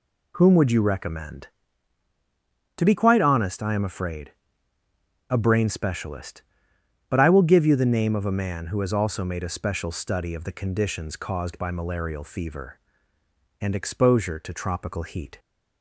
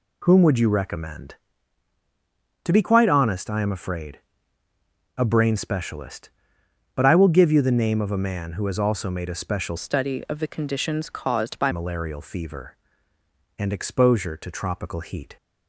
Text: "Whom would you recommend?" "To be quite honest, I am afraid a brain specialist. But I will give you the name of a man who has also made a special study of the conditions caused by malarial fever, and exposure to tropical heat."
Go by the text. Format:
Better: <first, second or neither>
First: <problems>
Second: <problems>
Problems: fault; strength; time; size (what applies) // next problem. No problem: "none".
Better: first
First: pauses between "afraid" and "a"; noticeable; at 4.3 s; 0.96 s long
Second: pauses between "afraid" and "a"; noticeable; at 4.2 s; 0.96 s long // changes voice from "study" to "by"; from 9.7 to 11.7 s; 2.0 s long